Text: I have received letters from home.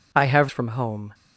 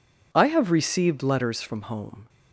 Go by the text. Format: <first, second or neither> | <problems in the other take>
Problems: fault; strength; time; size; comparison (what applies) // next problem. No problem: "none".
second | skips "received letters"; at 0.4 s